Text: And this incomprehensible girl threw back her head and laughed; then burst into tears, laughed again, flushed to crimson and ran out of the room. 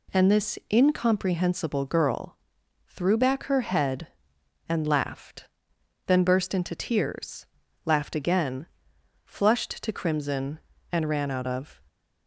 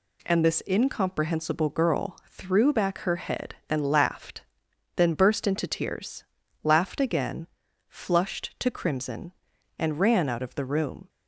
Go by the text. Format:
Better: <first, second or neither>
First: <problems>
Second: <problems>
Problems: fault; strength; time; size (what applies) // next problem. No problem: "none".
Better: second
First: pauses between "girl" and "threw"; noticeable; at 2.3 s; 0.52 s long // stops before "the room"; at 11.8 s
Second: none